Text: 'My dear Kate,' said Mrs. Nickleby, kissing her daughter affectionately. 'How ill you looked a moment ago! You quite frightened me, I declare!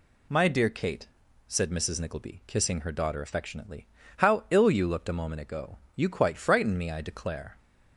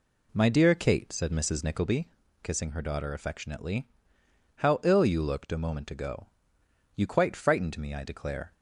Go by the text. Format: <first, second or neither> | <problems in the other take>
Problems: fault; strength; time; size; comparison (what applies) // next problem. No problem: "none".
first | starts louder than the rest; slight; until 2.0 s; 2.5 dB